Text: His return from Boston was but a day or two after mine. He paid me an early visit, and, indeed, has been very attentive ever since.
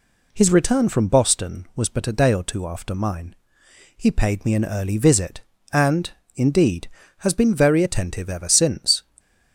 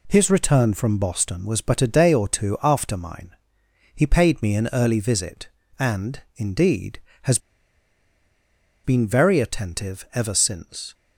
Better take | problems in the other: first | pauses between "has" and "been"; strong; at 7.3 s; 1.4 s long

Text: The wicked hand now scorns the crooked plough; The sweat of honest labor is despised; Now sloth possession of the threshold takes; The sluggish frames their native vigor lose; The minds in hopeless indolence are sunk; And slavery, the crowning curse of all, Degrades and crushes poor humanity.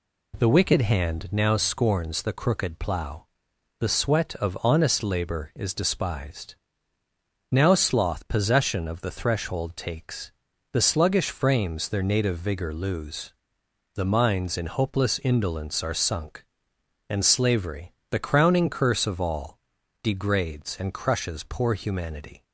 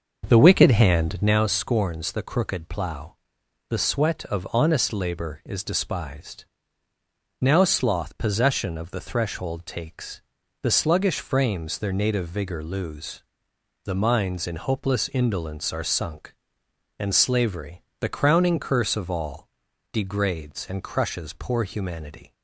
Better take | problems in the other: first | starts louder than the rest; until 1.4 s; 6.5 dB

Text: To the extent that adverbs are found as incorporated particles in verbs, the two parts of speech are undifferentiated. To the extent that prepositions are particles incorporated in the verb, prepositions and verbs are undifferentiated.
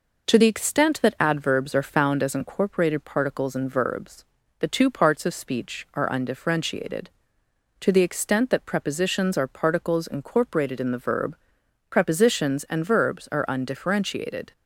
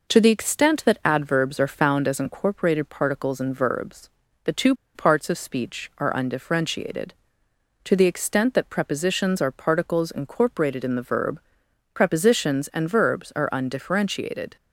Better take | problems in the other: first | pauses between "two" and "parts"; slight; at 4.7 s; 0.22 s long

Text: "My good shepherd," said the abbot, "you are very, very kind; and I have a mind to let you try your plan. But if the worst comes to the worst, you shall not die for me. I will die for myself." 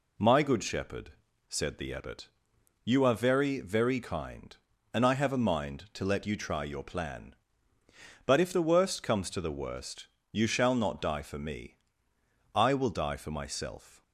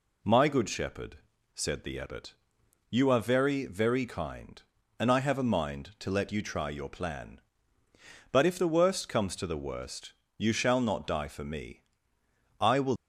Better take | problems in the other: first | stops before "die for myself"; at 12.9 s

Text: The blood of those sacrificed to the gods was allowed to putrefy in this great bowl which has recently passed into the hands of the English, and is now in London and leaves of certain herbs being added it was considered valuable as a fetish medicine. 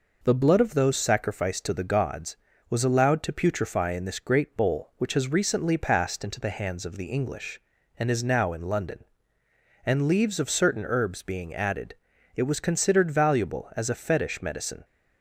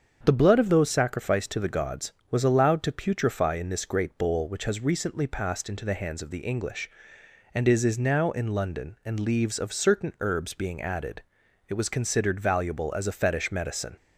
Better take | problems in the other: first | starts louder than the rest; strong; until 1.2 s; 7 dB // says "is" twice; at 7.8 s // pauses between "added" and "it"; at 11.2 s; 0.44 s long; also in the first

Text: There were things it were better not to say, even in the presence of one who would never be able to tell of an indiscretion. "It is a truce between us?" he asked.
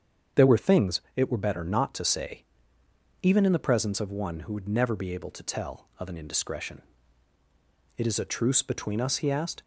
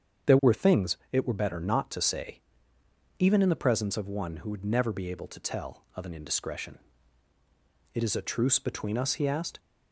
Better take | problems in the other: neither | starts louder than the rest; strong; the same in both // pauses between "things" and "it"; slight; the same in both

